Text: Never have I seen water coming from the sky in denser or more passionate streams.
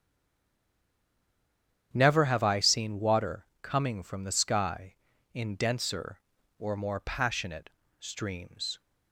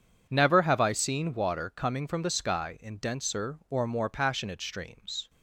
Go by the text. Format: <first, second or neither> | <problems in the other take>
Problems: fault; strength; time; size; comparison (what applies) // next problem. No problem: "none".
second | stays silent before the first word; noticeable; until 1.9 s; 1.9 s long // starts louder than the rest; strong; until 2.9 s; 9 dB // pauses between "water" and "coming"; slight; at 3.4 s; 0.18 s long // pauses between "passionate" and "streams"; slight; at 7.6 s; 0.30 s long